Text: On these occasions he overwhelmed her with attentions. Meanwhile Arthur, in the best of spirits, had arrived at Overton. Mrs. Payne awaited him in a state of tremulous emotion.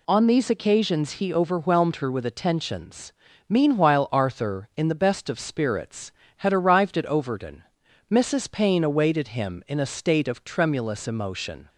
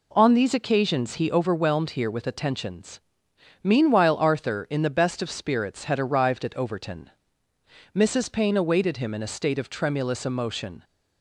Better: first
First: none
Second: says "here" for "her"; at 1.9 s

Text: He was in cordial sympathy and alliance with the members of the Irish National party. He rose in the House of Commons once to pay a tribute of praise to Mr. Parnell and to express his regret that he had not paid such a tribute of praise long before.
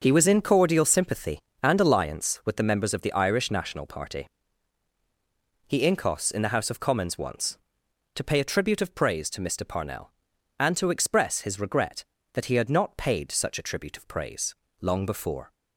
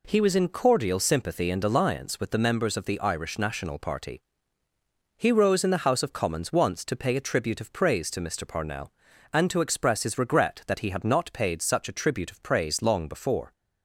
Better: second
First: starts louder than the rest; until 1.0 s; 6 dB // says "incos" for "rose"; at 5.8 s // pauses between "praise" and "long"; slight; at 14.5 s; 0.24 s long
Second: none

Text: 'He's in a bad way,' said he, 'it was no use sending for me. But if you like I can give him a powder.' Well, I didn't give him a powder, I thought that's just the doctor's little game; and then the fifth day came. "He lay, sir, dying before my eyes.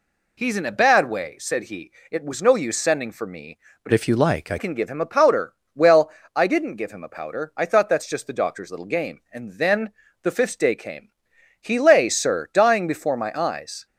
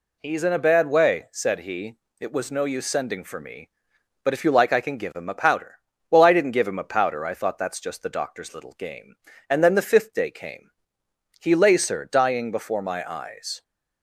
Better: second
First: changes voice from "if" to "I"; from 3.9 to 4.5 s; 0.6 s long // pauses between "then" and "the"; slight; at 9.8 s; 0.32 s long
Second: none

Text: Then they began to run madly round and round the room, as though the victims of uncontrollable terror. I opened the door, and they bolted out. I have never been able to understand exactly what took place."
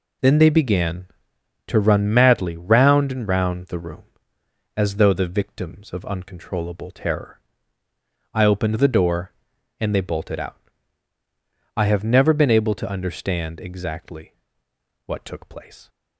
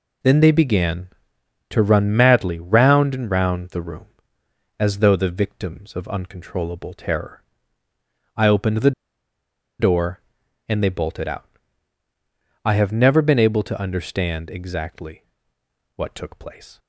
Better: first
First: pauses between "exactly" and "what"; noticeable; at 14.3 s; 0.72 s long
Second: pauses between "the" and "door"; noticeable; at 8.9 s; 0.88 s long // pauses between "exactly" and "what"; noticeable; at 15.2 s; 0.72 s long

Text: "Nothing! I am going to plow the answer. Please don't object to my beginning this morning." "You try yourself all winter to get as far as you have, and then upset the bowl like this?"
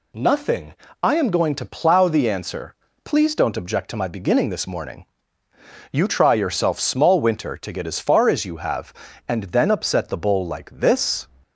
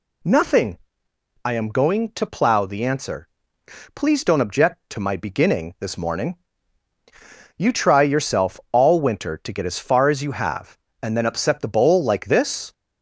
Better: second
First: says "small" for "all"; at 6.7 s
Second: none

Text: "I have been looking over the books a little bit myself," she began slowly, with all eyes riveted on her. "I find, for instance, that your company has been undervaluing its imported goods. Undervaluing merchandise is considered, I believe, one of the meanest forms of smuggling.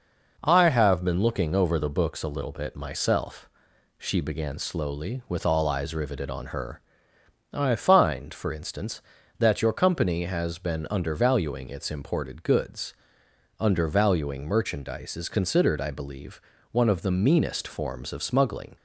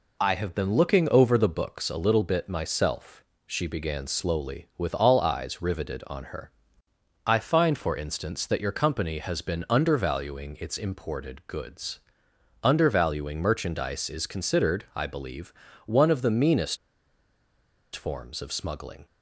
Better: first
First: none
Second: pauses between "meanest" and "forms"; at 16.7 s; 1.1 s long

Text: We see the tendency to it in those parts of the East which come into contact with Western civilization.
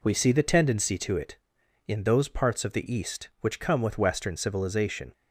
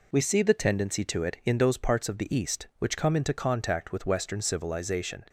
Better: second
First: skips "into contact"; at 3.8 s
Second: none

